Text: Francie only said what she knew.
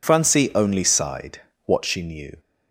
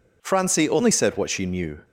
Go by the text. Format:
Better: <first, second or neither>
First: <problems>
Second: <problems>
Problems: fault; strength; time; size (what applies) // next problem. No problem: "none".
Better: second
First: says "sighed" for "said"; at 0.8 s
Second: none